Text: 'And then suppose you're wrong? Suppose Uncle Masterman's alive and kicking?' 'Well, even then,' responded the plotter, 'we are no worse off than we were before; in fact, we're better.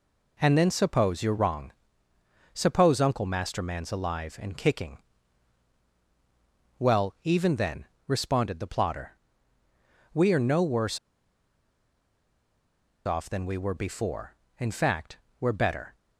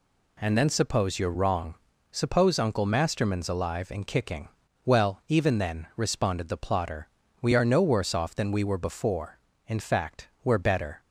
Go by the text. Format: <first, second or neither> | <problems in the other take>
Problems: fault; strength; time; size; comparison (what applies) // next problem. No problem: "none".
second | pauses between "worse" and "off"; strong; at 10.9 s; 2.0 s long